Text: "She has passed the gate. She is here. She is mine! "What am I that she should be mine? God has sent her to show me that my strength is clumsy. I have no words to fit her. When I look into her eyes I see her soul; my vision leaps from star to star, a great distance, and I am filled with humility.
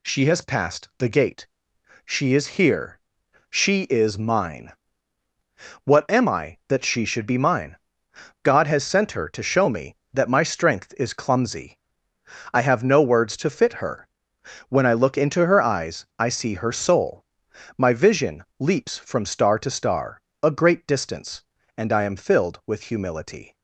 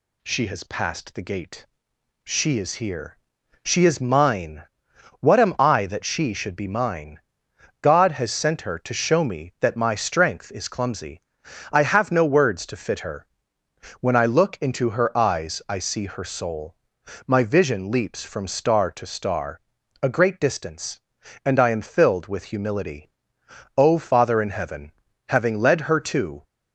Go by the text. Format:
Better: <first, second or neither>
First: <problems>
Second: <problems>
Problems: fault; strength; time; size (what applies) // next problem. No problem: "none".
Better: first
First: none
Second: goes on to say "O Father in Heaven having led her to"; strong; from 23.7 s on; 2.6 s long